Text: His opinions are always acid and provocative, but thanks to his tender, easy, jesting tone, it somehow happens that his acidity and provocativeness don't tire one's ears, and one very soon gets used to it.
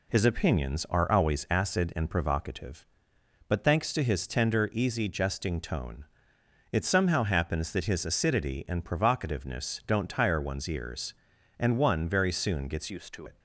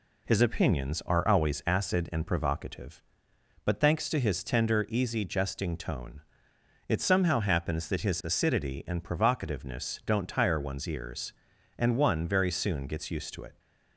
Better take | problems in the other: second | changes voice from "used" to "to"; from 12.8 to 13.2 s; 0.4 s long

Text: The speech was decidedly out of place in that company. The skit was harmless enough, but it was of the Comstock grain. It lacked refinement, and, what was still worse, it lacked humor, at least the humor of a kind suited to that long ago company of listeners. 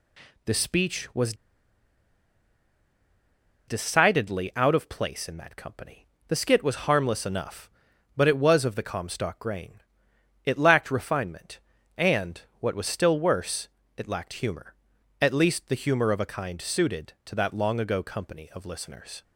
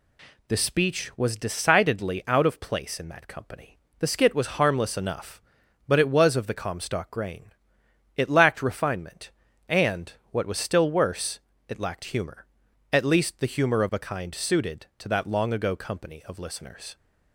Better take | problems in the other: second | pauses between "was" and "decidedly"; strong; at 1.3 s; 2.3 s long

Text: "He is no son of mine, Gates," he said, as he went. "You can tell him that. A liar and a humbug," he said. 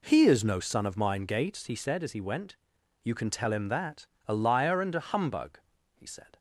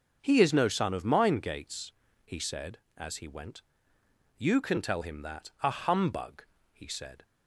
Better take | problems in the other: first | starts louder than the rest; until 1.2 s; 6 dB // skips "A liar and"; at 5.5 s

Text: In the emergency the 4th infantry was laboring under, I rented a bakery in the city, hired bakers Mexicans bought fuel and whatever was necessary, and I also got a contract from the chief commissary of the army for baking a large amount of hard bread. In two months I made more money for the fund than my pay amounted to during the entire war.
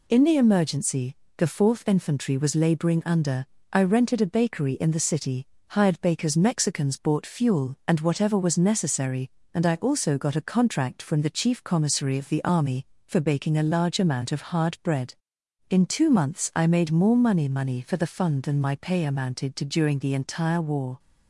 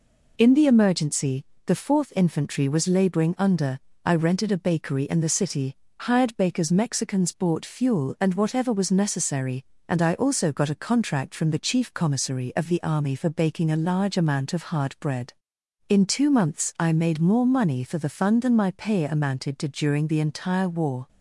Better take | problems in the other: second | pauses between "emergency" and "the"; slight; at 1.1 s; 0.22 s long; slight in the second // says "money" twice; at 17.4 s

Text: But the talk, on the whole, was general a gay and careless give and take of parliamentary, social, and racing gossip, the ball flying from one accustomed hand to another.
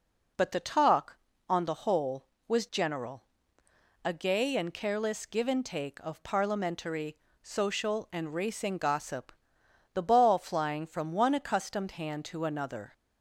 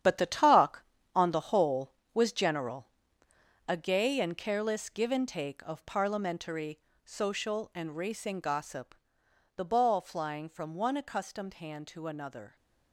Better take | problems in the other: first | gets quieter; strong; throughout; 10 dB // pauses between "general" and "a"; noticeable; at 2.8 s; 0.82 s long; noticeable in the first

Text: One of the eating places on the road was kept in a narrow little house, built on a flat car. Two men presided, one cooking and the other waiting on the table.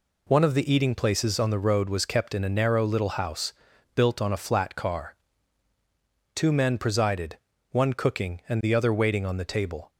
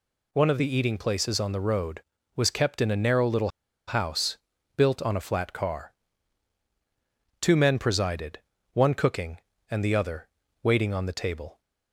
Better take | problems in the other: first | pauses between "little" and "house"; at 3.4 s; 0.38 s long // pauses between "other" and "waiting"; slight; at 10.2 s; 0.36 s long

